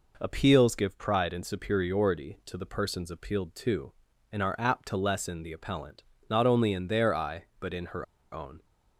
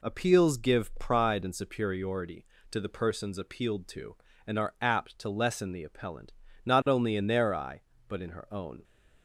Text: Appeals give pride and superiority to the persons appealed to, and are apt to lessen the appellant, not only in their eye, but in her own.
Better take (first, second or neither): second